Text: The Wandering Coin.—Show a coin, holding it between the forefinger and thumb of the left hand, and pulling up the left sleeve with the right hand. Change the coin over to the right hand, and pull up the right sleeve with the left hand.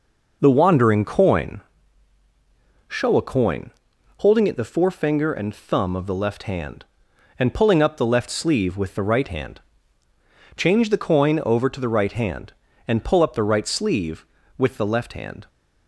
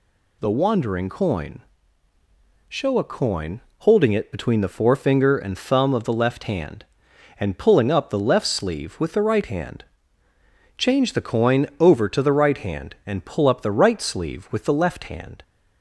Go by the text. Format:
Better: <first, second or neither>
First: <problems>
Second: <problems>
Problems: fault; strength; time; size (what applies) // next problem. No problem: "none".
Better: second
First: skips "between"; at 4.5 s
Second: none